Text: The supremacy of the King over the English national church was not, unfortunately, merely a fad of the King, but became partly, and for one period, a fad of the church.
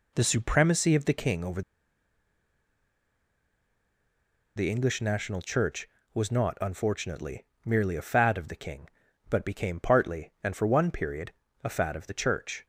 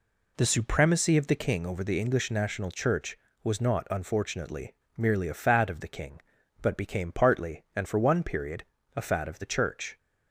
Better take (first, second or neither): second